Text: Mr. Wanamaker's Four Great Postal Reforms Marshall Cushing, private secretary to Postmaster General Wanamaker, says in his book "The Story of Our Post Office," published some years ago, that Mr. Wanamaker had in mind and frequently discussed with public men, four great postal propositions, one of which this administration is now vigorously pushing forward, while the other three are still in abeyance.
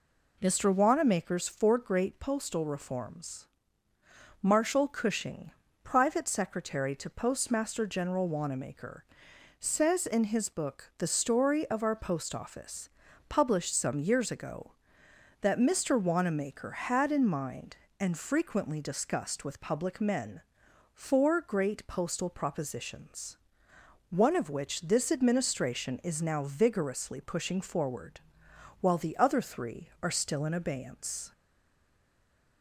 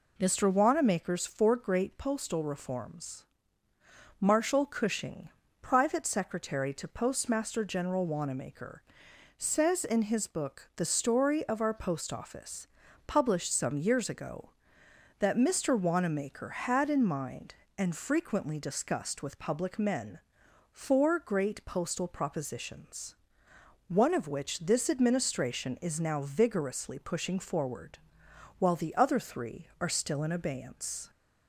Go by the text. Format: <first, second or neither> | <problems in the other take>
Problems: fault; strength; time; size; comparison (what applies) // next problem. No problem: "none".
second | pauses between "Reforms" and "Marshall"; noticeable; at 3.4 s; 0.92 s long; noticeable in the second // stays silent after the last word; noticeable; from 31.3 s on; 1.3 s long